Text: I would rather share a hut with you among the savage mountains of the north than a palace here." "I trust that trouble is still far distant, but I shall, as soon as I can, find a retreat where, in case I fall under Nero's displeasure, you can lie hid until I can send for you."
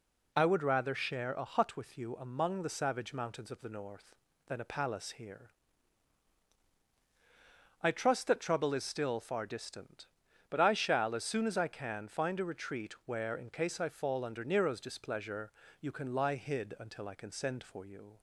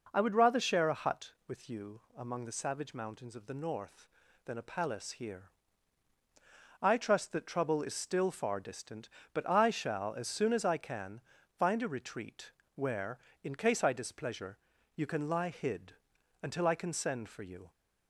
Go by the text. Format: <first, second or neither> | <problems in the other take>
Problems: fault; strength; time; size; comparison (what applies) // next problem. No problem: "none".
first | pauses between "retreat" and "where"; slight; at 12.5 s; 0.22 s long // skips "fall under Nero's"; at 13.9 s // pauses between "hid" and "until"; noticeable; at 15.9 s; 0.46 s long